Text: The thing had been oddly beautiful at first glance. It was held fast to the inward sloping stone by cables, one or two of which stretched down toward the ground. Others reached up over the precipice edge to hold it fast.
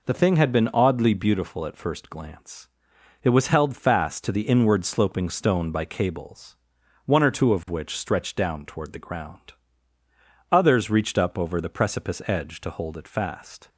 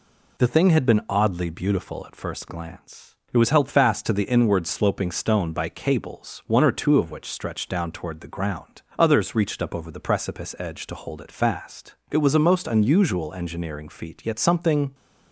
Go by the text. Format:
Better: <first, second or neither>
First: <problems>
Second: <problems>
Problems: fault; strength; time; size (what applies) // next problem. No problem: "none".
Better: first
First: none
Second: goes on to say "It was a most unusual engineering feat yet something"; strong; from 12.1 s on; 2.8 s long